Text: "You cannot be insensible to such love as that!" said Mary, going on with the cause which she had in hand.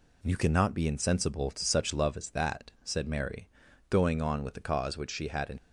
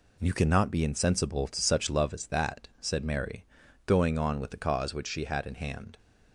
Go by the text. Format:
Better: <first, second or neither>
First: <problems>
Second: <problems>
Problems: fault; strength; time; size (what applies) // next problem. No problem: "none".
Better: second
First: stops before "hand"; at 5.5 s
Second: none